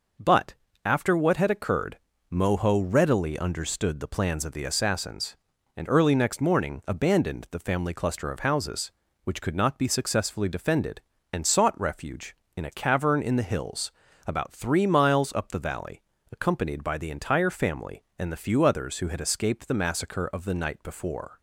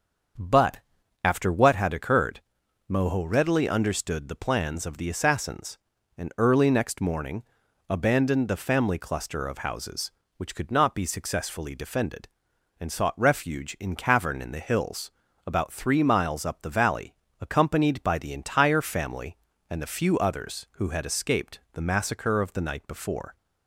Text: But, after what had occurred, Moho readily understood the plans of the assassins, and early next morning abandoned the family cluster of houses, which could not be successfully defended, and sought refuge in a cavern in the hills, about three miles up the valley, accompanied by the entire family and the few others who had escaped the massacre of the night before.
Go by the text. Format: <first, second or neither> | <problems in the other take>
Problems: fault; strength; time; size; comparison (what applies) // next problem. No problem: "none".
first | starts louder than the rest; until 1.8 s; 6.5 dB // pauses between "morning" and "abandoned"; noticeable; at 7.4 s; 0.46 s long // skips "a"; at 13.9 s